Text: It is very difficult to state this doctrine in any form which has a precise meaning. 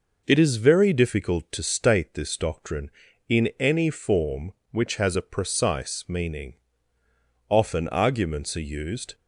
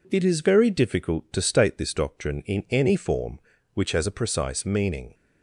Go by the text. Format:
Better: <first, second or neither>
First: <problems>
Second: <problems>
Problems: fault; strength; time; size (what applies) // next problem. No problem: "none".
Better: second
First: goes on to say "Often arguments are used"; from 7.4 s on; 1.6 s long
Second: none